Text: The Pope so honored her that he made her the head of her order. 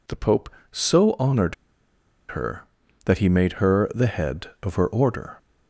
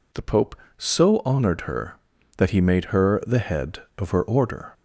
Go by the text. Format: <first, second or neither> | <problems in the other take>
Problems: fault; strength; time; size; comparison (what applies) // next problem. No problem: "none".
second | pauses between "honored" and "her"; noticeable; at 1.5 s; 0.75 s long